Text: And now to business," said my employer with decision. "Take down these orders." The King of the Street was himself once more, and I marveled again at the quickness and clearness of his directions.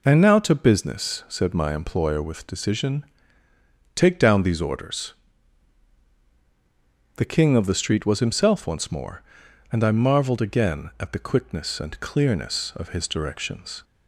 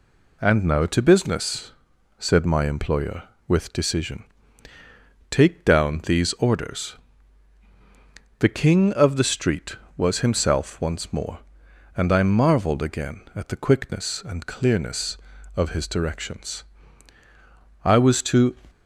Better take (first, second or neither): first